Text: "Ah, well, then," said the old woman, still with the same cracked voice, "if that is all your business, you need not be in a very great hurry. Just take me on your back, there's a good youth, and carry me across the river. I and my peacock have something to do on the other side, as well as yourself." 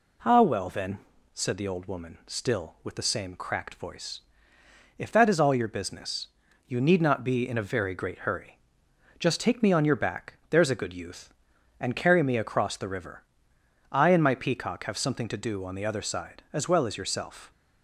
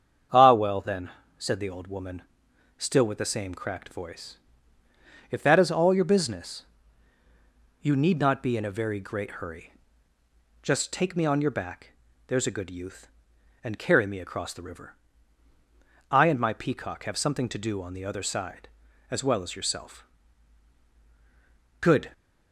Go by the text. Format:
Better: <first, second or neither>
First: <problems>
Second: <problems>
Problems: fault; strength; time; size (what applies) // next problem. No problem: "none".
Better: first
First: none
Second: starts louder than the rest; strong; until 1.6 s; 7.5 dB // goes on to say "Good"; slight; from 21.8 s on; 0.30 s long